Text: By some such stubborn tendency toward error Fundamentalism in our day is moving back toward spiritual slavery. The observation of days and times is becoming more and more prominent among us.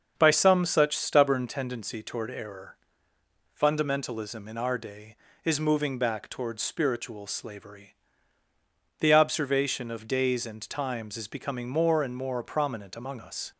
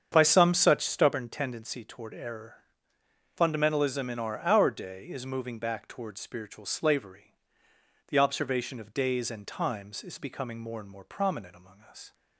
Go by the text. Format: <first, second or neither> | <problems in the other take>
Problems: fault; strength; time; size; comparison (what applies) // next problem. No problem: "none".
first | starts louder than the rest; strong; until 1.1 s; 7.5 dB; also in the first // pauses between "error" and "Fundamentalism"; noticeable; at 2.5 s; 0.78 s long; noticeable in the first // says "our" twice; at 4.4 s